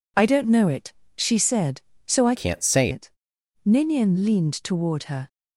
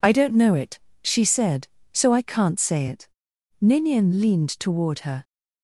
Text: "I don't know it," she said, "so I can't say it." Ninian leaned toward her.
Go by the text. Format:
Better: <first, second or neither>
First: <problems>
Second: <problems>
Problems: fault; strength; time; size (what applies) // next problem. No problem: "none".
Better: second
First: changes voice from "can't" to "say"; from 2.3 to 2.9 s; 0.6 s long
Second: none